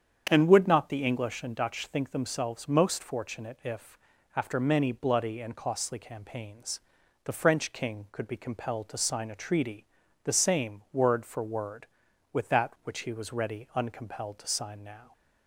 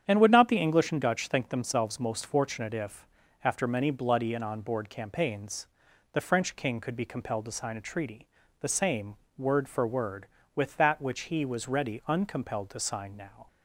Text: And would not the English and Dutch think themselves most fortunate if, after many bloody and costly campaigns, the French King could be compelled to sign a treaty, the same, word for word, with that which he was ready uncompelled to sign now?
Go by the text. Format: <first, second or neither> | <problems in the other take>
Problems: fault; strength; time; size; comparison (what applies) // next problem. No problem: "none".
first | starts louder than the rest; strong; until 1.0 s; 9 dB; strong in the first // says "onboard" for "costly"; at 4.4 s